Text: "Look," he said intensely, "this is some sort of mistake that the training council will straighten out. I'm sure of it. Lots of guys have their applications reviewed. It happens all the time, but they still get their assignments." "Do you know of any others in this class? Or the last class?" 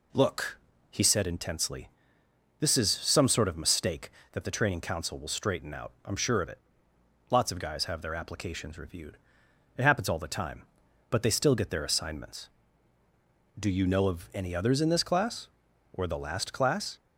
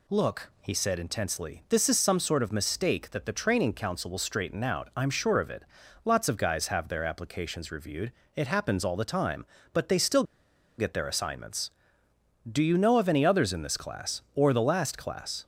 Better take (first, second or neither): first